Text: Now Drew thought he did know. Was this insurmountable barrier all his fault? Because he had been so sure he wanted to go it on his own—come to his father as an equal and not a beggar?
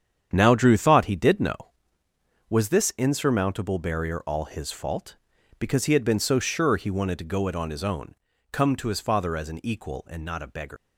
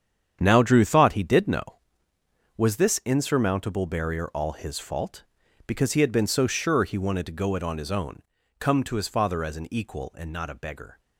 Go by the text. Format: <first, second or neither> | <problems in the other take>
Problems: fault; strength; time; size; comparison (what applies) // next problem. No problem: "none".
second | starts louder than the rest; strong; until 1.3 s; 8.5 dB; strong in the second // leaves "beggar" unfinished; at 10.7 s; 155 ms